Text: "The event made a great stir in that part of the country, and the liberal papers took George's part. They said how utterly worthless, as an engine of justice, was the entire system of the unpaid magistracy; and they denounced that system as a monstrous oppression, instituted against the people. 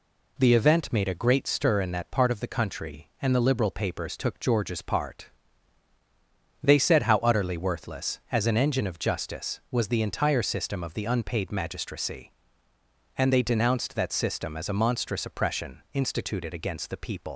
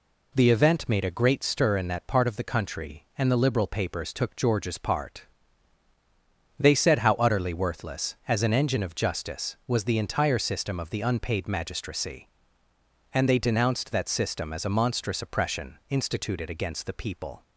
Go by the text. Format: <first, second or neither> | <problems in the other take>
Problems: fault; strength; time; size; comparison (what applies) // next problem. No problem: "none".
second | leaves "people" unfinished; at 17.3 s; 110 ms